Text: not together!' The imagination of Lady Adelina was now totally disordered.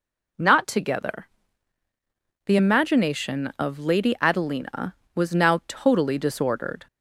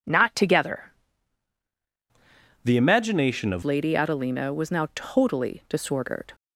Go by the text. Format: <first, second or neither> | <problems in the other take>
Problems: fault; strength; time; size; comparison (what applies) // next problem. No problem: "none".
first | changes voice from "The" to "of"; from 2.6 to 3.6 s; 1.0 s long